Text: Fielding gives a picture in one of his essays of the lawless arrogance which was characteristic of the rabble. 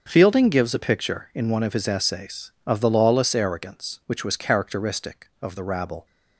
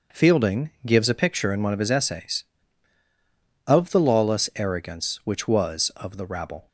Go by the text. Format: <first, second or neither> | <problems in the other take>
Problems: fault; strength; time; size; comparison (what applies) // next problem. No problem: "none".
first | starts louder than the rest; noticeable; until 1.3 s; 6 dB; also in the first // pauses between "Fielding" and "gives"; slight; at 0.6 s; 0.16 s long // skips "characteristic"; at 5.9 s